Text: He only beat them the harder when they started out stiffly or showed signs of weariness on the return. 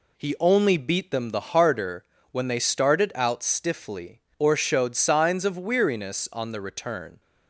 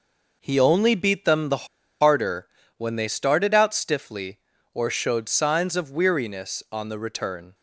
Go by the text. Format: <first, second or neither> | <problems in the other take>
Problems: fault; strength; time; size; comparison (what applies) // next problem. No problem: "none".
first | pauses between "the" and "harder"; slight; at 1.6 s; 0.35 s long // pauses between "harder" and "when"; slight; at 2.4 s; 0.30 s long; slight in the first